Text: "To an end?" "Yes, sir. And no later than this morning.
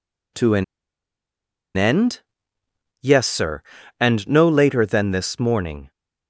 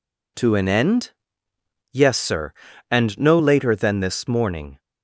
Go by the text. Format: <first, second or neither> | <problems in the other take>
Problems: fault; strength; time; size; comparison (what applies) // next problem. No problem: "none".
second | pauses between "an" and "end"; at 0.6 s; 1.1 s long